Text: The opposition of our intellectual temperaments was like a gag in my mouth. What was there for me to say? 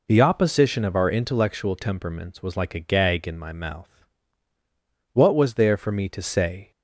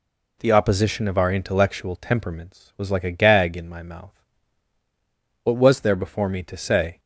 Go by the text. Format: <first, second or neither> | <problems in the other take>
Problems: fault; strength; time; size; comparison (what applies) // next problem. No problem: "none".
first | says "before" for "for"; at 5.9 s